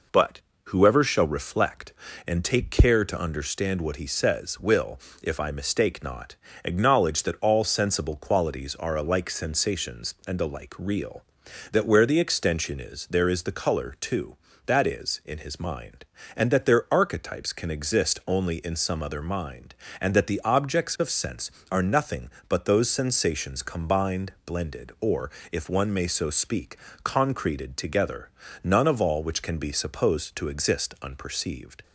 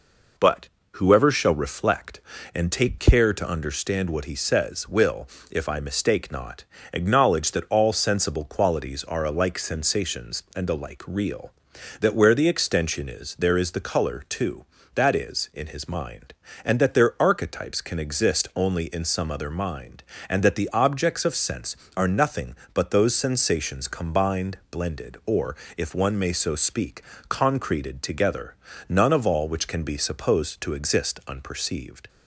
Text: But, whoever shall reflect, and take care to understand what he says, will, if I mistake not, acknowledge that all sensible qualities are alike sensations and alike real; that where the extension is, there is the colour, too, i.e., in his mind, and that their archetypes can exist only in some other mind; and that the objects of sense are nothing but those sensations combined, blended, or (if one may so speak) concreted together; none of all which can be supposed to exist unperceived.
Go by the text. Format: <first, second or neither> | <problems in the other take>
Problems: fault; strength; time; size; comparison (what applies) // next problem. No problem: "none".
neither | none